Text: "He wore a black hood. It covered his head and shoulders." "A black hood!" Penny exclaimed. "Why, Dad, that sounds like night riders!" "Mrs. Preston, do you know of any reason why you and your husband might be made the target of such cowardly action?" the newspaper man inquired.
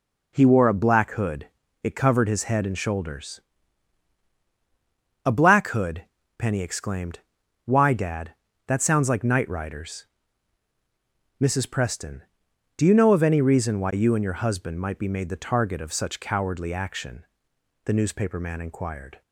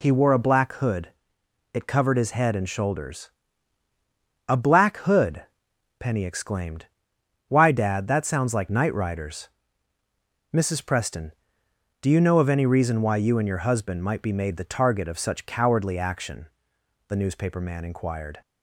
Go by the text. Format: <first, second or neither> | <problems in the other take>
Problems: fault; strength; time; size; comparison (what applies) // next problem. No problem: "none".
neither | none